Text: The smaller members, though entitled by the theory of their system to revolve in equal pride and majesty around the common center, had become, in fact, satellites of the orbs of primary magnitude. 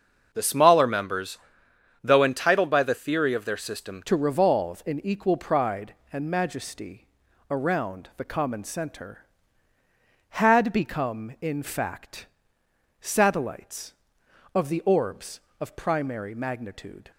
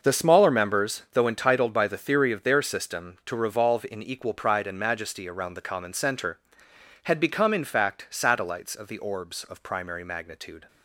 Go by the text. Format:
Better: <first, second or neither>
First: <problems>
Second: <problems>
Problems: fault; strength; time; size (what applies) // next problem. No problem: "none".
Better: second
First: starts louder than the rest; until 1.3 s; 6 dB // changes voice at "to"; from 4.0 s on; 13.1 s long // pauses between "majesty" and "around"; noticeable; at 7.0 s; 0.46 s long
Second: none